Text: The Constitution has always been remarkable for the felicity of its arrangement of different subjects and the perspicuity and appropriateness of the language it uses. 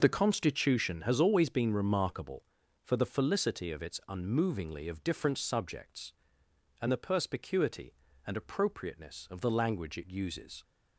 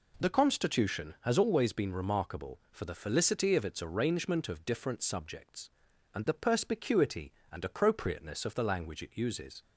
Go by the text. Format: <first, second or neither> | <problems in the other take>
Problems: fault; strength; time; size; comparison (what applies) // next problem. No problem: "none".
second | says "unmovingly" for "arrangement"; at 4.0 s